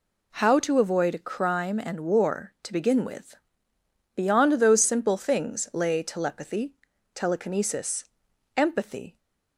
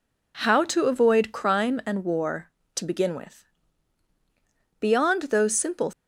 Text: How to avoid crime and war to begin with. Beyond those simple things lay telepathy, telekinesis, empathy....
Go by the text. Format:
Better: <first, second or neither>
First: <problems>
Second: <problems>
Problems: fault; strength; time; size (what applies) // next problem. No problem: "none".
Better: first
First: none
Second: stops before "things lay telepathy telekinesis empathy"; at 5.9 s